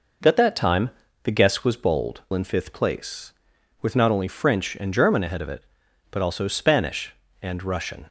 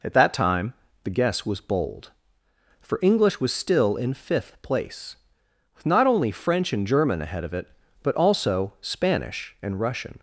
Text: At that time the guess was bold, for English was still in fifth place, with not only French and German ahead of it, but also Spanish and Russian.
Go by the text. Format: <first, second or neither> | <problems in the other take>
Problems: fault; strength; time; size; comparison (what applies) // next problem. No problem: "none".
second | pauses between "time" and "the"; slight; at 0.9 s; 0.32 s long; slight in the second // skips "for English was still"; at 2.2 s